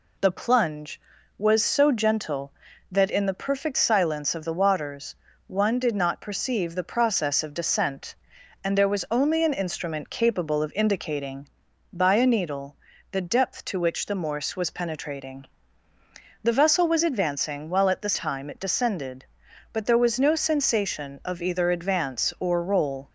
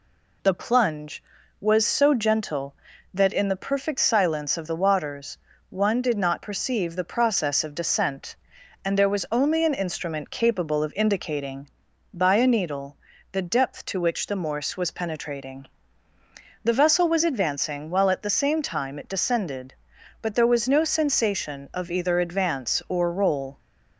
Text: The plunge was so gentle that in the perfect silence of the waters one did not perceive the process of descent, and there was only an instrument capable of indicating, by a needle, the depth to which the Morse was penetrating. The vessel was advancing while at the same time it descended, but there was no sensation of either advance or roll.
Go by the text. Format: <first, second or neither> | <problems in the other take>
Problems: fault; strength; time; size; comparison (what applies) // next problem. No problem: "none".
second | pauses between "waters" and "one"; slight; at 5.1 s; 0.32 s long; slight in the second // skips "same"; at 18.1 s